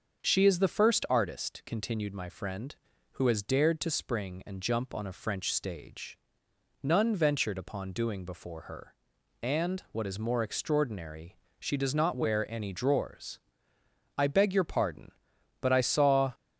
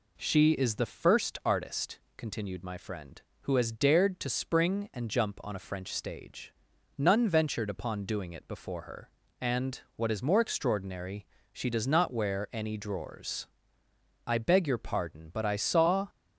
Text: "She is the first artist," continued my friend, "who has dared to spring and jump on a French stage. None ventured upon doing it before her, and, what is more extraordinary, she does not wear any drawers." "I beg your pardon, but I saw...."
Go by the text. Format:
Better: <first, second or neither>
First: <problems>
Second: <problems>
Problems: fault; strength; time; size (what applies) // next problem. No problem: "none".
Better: second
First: starts louder than the rest; until 1.2 s; 6.5 dB // skips "it"; at 8.2 s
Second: none